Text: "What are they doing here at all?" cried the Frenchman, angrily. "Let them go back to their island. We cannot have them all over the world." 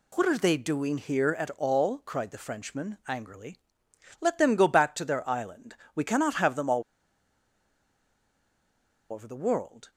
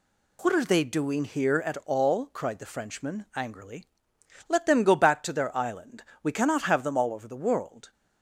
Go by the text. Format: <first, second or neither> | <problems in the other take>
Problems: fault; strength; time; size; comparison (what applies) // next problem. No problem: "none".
second | pauses between "all" and "over"; strong; at 6.8 s; 2.3 s long